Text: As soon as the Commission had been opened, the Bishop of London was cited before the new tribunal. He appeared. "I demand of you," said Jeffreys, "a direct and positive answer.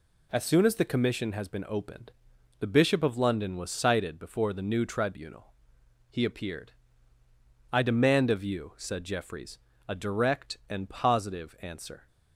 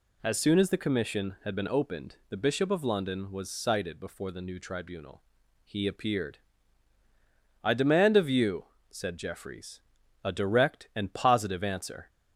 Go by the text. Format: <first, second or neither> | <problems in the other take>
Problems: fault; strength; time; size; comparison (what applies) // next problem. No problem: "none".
second | says "has" for "had"; at 1.3 s